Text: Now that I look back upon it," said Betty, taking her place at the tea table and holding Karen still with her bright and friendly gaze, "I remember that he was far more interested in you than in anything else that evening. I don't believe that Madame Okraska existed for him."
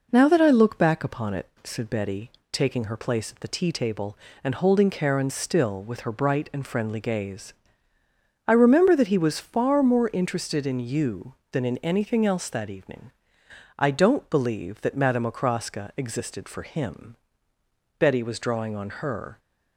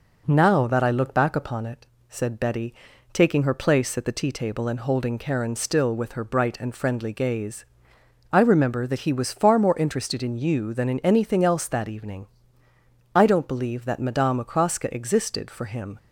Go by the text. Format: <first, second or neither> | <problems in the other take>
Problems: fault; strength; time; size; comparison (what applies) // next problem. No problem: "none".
second | goes on to say "Betty was drawing on her"; from 17.9 s on; 1.4 s long